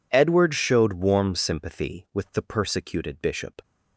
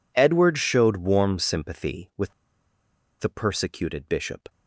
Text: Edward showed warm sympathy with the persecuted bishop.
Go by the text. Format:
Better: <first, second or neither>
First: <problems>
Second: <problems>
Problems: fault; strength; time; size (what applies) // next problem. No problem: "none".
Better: first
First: none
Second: pauses between "with" and "the"; noticeable; at 2.3 s; 0.88 s long